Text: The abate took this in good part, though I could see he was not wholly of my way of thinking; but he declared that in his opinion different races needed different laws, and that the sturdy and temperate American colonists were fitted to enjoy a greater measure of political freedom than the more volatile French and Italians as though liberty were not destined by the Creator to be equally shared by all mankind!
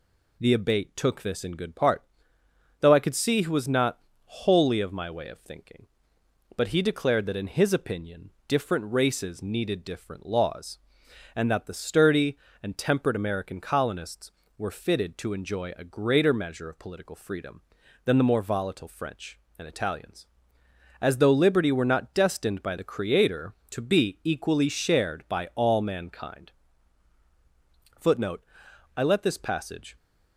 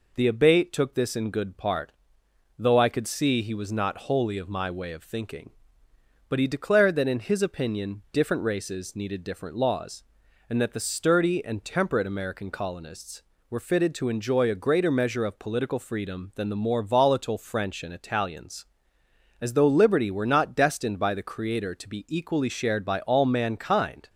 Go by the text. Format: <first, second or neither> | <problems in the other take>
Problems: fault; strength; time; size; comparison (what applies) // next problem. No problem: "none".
second | pauses between "not" and "wholly"; slight; at 3.9 s; 0.28 s long // pauses between "opinion" and "different"; slight; at 8.2 s; 0.16 s long // goes on to say "Footnote I let this passage"; strong; from 27.9 s on; 1.9 s long